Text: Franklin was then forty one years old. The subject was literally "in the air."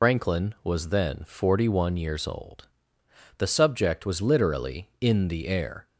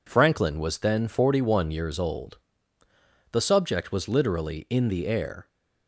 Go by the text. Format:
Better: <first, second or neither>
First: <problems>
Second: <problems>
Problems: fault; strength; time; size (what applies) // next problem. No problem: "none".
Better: second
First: loses the start of "Franklin"; at 0.0 s; 125 ms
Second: none